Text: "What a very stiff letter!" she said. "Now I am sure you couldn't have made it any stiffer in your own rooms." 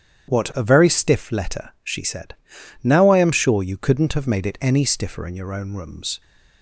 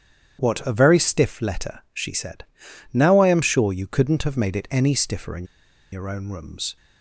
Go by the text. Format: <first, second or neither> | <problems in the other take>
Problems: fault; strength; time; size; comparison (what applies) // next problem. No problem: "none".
first | starts louder than the rest; strong; until 1.4 s; 9 dB; strong in the first // pauses between "in" and "your"; noticeable; at 5.4 s; 0.48 s long